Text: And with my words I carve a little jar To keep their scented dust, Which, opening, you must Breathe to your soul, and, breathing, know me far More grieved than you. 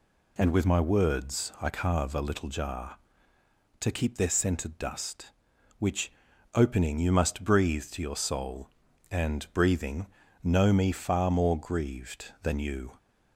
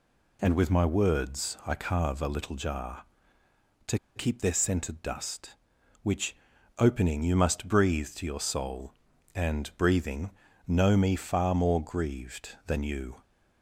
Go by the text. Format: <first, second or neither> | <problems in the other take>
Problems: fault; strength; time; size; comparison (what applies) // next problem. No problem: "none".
first | pauses between "To" and "keep"; slight; at 3.9 s; 0.17 s long